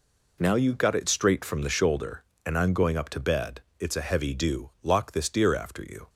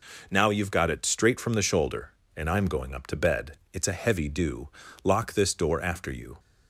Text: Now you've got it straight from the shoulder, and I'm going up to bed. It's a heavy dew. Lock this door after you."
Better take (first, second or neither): second